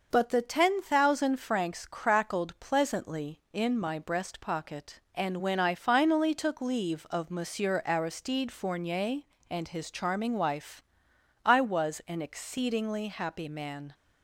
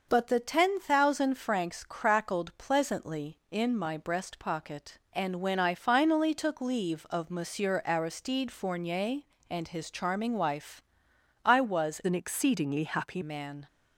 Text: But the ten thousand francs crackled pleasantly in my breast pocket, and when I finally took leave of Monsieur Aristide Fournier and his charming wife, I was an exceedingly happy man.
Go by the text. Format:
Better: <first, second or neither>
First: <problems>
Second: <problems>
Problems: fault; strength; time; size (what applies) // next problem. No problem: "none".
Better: first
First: starts louder than the rest; noticeable; until 1.1 s; 6 dB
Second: starts louder than the rest; noticeable; until 1.1 s; 6 dB // changes voice from "an" to "happy"; from 12.0 to 13.2 s; 1.2 s long